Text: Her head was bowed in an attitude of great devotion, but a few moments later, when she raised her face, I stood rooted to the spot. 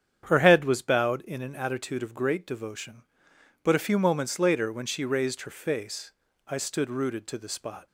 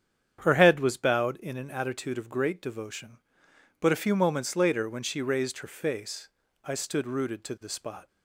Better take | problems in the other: neither | starts louder than the rest; strong; the same in both

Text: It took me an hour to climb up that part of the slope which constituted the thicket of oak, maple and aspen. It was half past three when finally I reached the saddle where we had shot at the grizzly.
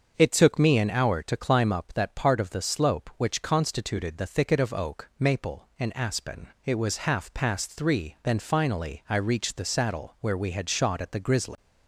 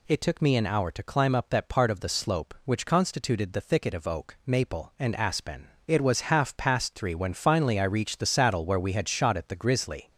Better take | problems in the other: second | starts louder than the rest; until 1.1 s; 6.5 dB // says "then" for "when"; at 8.2 s

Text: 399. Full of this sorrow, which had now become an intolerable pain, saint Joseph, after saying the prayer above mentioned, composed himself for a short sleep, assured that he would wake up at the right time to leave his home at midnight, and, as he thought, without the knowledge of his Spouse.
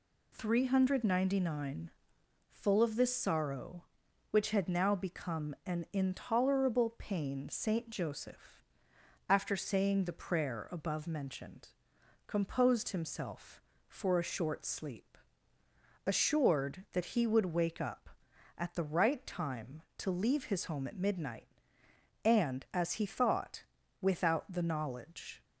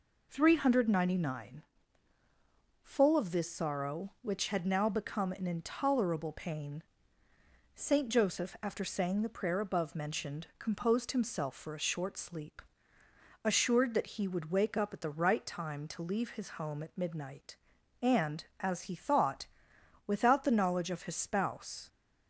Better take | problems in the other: second | stops before "of his Spouse"; at 25.4 s

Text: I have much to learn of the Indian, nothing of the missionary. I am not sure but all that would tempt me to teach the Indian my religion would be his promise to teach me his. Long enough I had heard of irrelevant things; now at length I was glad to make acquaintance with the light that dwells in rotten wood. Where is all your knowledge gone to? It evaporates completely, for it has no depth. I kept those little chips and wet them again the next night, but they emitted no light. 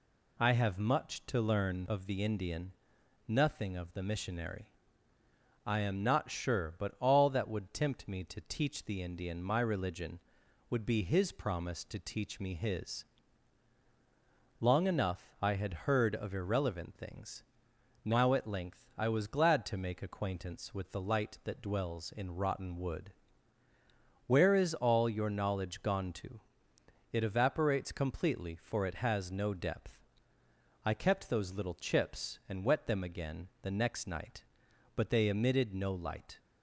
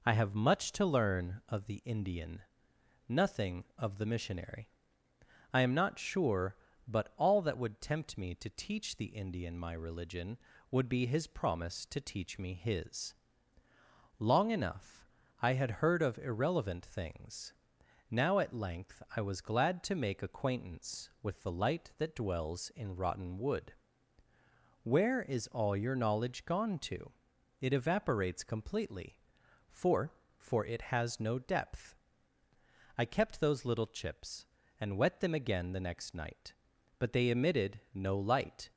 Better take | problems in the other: first | pauses between "enough" and "I"; slight; at 15.0 s; 0.34 s long // says "for" twice; at 30.3 s

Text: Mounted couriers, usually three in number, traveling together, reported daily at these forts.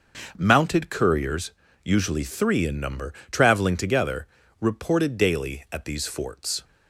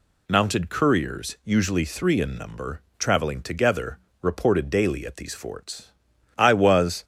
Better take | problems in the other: first | goes on to say "I was"; noticeable; from 6.3 s on; 0.66 s long

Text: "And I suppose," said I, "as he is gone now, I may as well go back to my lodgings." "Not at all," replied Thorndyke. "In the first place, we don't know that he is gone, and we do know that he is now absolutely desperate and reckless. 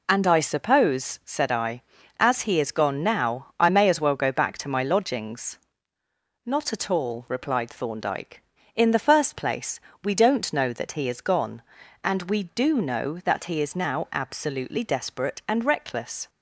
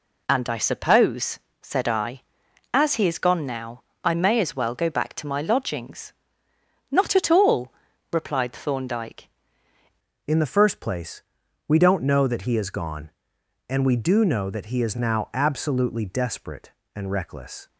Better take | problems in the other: first | changes voice at "In"; from 10.2 s on; 7.4 s long

